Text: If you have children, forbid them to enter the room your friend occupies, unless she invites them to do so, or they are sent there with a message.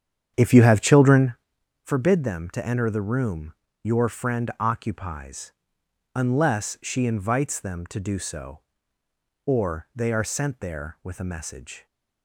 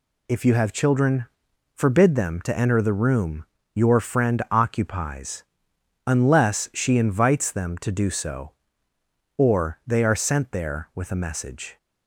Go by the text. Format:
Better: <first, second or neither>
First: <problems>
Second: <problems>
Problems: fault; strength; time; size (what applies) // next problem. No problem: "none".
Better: second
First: starts louder than the rest; strong; until 1.4 s; 8.5 dB // pauses between "room" and "your"; slight; at 3.5 s; 0.30 s long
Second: pauses between "room" and "your"; slight; at 3.4 s; 0.30 s long